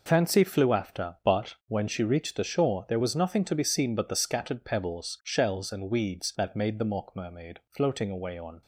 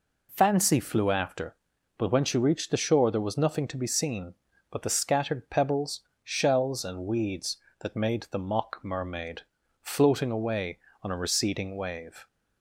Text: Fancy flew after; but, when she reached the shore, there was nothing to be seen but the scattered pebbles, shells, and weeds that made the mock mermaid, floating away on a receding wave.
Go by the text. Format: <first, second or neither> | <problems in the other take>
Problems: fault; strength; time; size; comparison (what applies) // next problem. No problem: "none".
second | stops before "a receding wave"; at 8.6 s